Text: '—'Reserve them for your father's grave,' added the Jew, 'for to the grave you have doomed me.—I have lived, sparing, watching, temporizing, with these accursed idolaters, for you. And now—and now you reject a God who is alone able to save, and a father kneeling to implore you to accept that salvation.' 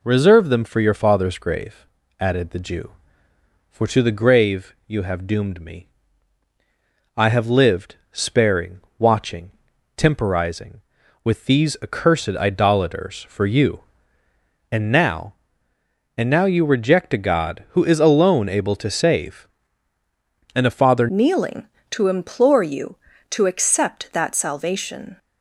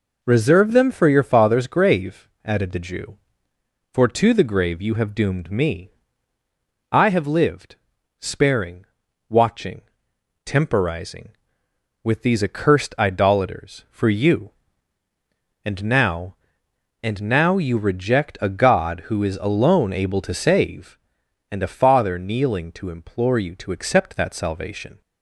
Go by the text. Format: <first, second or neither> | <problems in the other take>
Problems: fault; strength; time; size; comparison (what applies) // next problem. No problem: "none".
second | changes voice at "kneeling"; from 21.0 s on; 4.1 s long